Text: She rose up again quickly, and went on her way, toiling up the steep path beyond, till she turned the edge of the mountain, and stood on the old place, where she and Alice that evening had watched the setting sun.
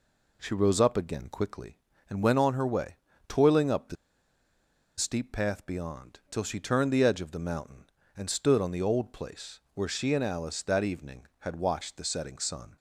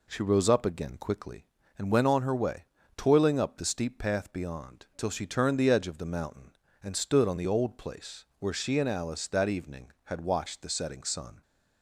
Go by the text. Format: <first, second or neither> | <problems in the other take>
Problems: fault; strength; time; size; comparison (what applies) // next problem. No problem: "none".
second | pauses between "the" and "steep"; at 3.9 s; 1.0 s long